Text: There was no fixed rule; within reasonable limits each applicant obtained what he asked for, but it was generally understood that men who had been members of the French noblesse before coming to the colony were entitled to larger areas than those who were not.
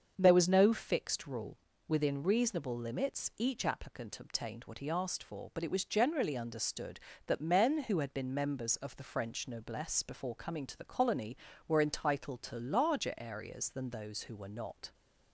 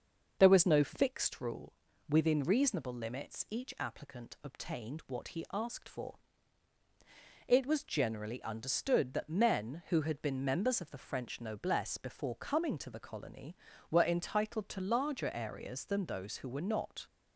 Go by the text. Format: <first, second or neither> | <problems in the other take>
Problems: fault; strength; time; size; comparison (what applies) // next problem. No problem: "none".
first | starts louder than the rest; until 1.4 s; 6.5 dB; also in the first // skips "but"; at 6.8 s